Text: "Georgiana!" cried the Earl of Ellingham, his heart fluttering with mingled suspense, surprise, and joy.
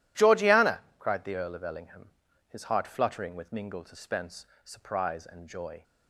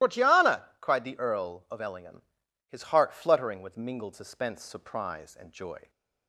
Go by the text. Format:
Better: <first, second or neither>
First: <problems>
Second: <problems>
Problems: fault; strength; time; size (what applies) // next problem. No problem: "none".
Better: first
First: none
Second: loses the start of "Georgiana"; at 0.0 s; 115 ms // starts louder than the rest; strong; until 1.1 s; 15.5 dB